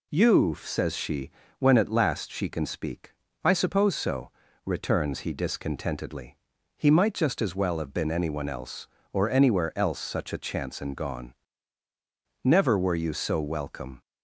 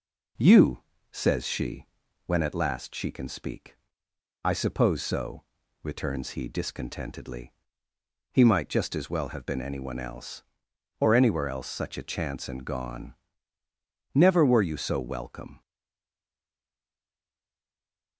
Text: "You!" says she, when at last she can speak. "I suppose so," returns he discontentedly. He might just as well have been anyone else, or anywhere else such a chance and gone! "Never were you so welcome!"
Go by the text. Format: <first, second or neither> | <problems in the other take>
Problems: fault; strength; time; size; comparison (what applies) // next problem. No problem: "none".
first | stays silent after the last word; strong; from 15.6 s on; 2.5 s long